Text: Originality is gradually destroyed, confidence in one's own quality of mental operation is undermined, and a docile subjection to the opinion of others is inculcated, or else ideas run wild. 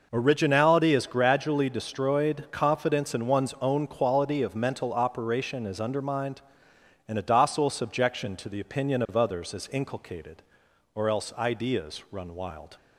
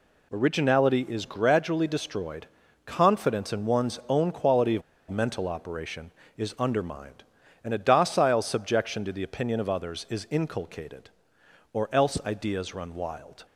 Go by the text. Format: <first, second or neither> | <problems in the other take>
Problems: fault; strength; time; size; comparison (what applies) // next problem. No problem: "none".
first | pauses between "of" and "mental"; slight; at 4.8 s; 0.27 s long